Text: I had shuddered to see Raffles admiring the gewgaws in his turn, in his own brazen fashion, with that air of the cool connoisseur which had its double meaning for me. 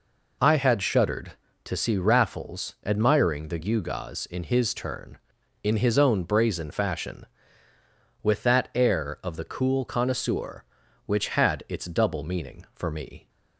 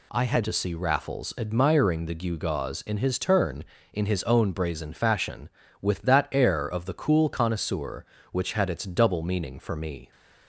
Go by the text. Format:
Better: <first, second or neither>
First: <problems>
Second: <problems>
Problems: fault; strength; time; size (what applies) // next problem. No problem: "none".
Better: first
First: none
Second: skips "shuddered"; at 0.4 s